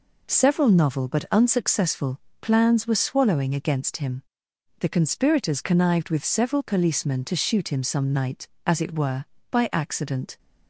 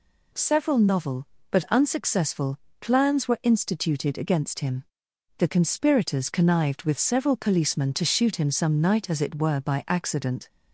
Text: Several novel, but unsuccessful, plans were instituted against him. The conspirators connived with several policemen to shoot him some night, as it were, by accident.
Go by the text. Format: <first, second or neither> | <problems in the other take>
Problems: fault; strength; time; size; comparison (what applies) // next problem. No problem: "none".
second | says "swallowing" for "instituted"; at 2.9 s